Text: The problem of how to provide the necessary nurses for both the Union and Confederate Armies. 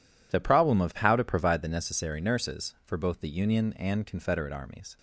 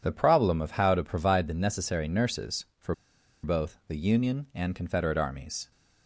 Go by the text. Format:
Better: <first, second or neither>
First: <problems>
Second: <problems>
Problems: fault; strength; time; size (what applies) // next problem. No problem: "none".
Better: first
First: none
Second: pauses between "for" and "both"; noticeable; at 2.9 s; 0.49 s long